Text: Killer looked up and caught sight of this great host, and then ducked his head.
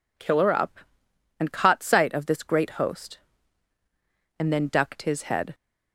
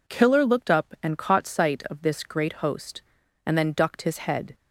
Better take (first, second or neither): second